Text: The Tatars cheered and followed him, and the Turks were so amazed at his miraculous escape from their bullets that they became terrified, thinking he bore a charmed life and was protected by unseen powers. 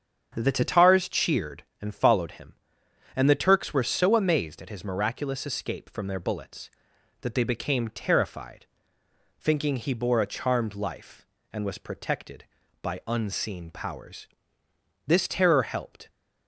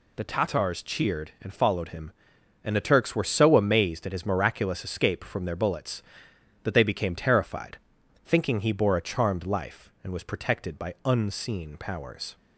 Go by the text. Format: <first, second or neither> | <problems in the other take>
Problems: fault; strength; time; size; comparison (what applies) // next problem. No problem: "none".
second | starts louder than the rest; strong; until 1.3 s; 8 dB // goes on to say "This terror helped"; noticeable; from 15.0 s on; 1.0 s long